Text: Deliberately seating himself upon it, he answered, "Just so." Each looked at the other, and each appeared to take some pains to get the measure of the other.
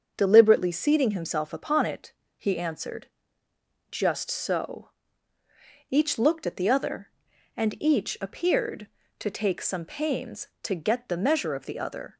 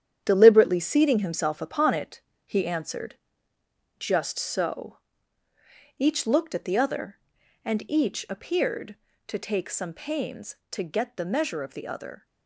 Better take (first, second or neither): first